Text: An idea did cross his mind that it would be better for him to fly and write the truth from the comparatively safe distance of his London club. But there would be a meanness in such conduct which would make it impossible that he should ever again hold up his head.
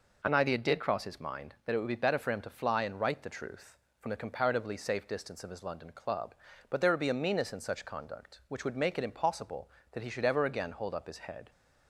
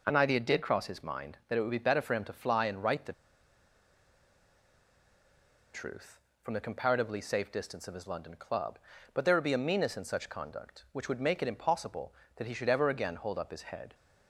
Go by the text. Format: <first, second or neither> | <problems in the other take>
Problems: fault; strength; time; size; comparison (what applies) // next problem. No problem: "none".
first | pauses between "the" and "truth"; strong; at 3.1 s; 2.6 s long